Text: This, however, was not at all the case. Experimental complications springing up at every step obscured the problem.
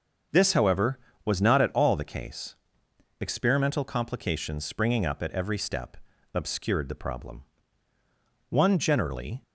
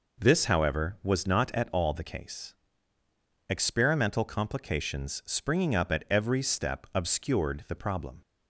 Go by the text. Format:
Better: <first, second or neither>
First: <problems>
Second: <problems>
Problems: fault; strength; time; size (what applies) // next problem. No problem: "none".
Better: second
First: starts louder than the rest; until 1.5 s; 6.5 dB // pauses between "step" and "obscured"; at 5.9 s; 0.38 s long // goes on to say "One generally"; noticeable; from 8.4 s on; 0.92 s long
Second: none